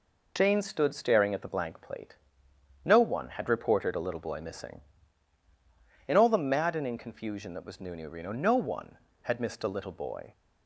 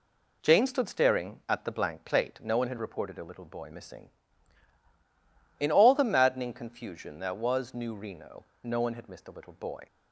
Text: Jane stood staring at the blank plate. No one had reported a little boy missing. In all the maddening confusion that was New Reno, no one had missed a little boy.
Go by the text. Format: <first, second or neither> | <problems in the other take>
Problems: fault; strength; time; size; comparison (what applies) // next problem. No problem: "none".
second | says "New" twice; at 7.9 s